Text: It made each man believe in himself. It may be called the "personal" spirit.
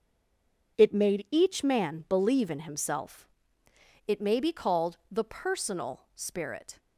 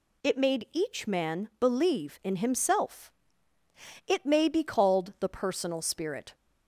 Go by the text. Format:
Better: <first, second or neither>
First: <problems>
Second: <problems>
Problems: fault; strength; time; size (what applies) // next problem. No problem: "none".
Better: second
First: stays silent before the first word; slight; until 0.7 s; 0.7 s long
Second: none